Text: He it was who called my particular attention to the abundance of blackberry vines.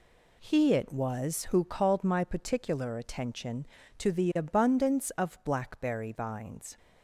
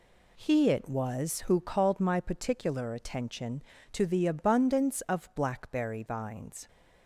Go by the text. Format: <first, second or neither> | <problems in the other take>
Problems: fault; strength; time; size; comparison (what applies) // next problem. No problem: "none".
neither | none